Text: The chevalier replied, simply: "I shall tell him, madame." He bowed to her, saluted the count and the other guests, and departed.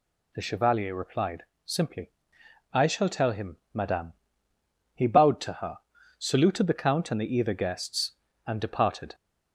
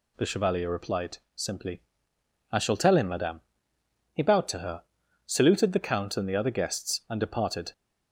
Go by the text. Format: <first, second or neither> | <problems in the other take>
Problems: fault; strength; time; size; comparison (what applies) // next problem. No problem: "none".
second | says "either" for "other"; at 7.3 s